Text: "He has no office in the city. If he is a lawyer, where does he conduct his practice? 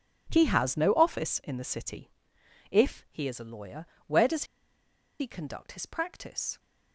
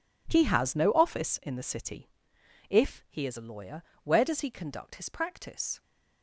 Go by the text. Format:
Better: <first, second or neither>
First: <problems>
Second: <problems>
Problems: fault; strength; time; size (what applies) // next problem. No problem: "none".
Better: second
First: pauses between "does" and "he"; noticeable; at 4.4 s; 0.75 s long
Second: none